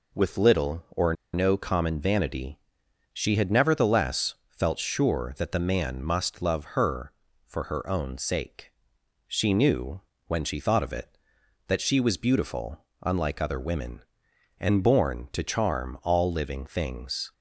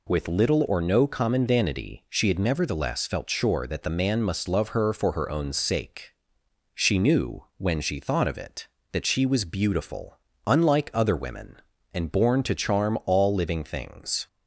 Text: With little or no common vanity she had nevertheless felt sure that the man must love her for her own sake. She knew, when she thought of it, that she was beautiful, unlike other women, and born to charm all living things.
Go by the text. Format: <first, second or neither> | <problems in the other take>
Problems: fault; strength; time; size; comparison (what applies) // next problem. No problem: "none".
second | pauses between "or" and "no"; slight; at 1.1 s; 0.19 s long // pauses between "vanity" and "she"; noticeable; at 2.5 s; 0.56 s long